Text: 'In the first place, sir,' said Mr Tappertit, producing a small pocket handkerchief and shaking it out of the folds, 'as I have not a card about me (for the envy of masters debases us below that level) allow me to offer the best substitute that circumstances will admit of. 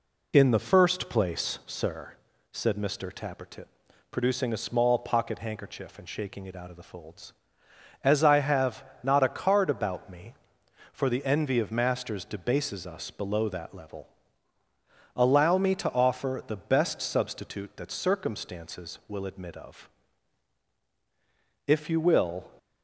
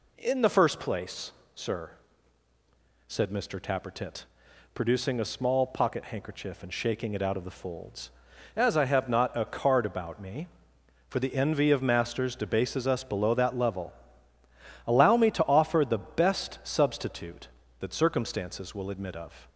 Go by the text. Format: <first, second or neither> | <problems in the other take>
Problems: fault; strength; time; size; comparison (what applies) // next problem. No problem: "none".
second | pauses between "have" and "not"; slight; at 8.8 s; 0.18 s long // goes on to say "If you will"; noticeable; from 21.6 s on; 0.86 s long